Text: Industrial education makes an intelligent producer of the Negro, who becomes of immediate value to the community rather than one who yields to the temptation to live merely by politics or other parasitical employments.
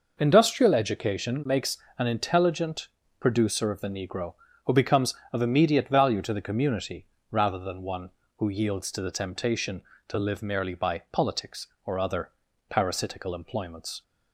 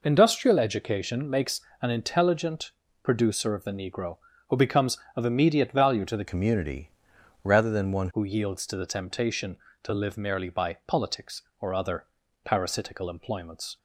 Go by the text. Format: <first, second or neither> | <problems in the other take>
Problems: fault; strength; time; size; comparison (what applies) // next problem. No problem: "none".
first | pauses between "makes" and "an"; slight; at 1.5 s; 0.20 s long; slight in the first // pauses between "intelligent" and "producer"; slight; at 2.7 s; 0.32 s long; slight in the first // changes voice from "community" to "one"; from 6.2 to 8.0 s; 1.8 s long // pauses between "community" and "rather"; noticeable; at 6.9 s; 0.52 s long; slight in the first // pauses between "other" and "parasitical"; at 12.0 s; 0.38 s long; also in the first